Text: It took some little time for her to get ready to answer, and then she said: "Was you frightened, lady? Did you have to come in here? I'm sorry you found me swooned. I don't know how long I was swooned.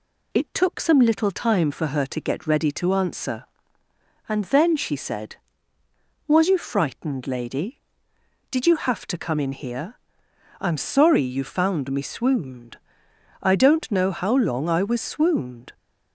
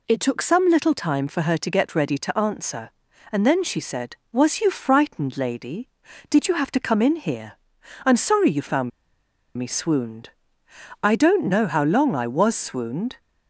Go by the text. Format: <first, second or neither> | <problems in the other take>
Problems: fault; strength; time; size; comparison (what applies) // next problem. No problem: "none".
first | pauses between "found" and "me"; noticeable; at 8.9 s; 0.68 s long